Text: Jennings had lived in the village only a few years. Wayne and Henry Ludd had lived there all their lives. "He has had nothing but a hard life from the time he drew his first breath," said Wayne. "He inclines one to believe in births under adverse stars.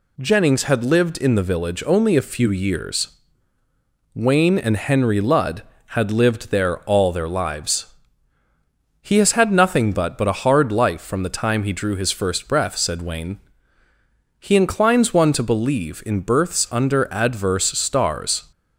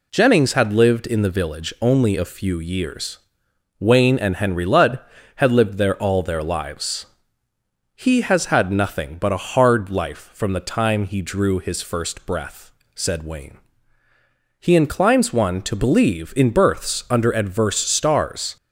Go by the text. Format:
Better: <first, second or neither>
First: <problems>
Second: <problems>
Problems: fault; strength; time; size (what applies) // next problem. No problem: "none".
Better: second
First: says "but" twice; at 10.1 s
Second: none